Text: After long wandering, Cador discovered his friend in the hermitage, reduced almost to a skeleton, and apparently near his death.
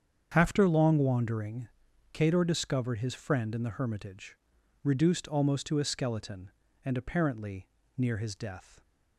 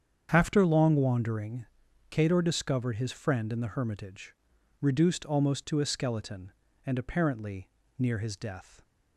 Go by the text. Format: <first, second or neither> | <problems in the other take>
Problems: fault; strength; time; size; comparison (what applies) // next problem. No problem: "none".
neither | starts louder than the rest; strong; the same in both // pauses between "apparently" and "near"; slight; the same in both